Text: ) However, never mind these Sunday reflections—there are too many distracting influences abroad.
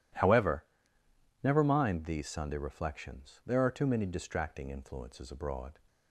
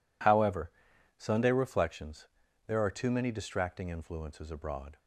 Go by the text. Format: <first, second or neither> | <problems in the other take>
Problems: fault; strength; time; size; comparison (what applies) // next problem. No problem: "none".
first | skips "never mind these"; at 0.9 s